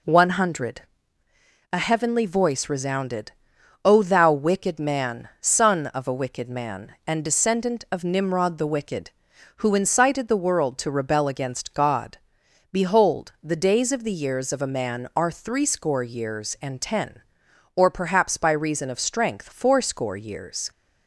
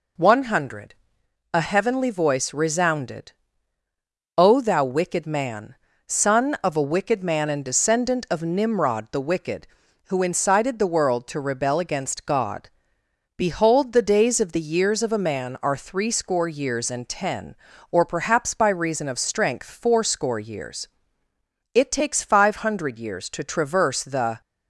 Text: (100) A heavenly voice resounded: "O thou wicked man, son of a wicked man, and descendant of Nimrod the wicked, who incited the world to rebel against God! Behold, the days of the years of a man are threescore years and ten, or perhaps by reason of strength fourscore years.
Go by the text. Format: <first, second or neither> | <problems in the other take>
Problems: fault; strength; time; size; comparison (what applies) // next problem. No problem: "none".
first | goes on to say "It takes five hundred years to traverse the"; strong; from 21.7 s on; 2.6 s long